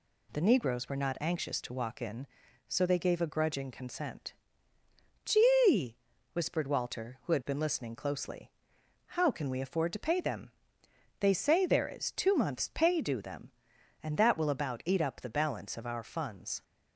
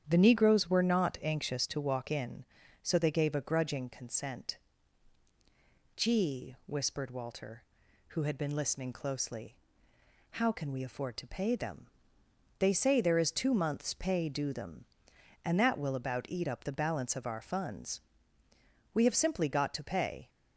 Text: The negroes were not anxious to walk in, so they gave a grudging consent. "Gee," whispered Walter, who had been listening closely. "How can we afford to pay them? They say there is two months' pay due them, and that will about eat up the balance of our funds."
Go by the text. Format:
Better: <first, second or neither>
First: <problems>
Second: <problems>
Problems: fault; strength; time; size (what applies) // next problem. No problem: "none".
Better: first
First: none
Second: starts louder than the rest; strong; until 1.0 s; 9 dB // goes on to say "We have simply got to pay"; from 18.9 s on; 1.3 s long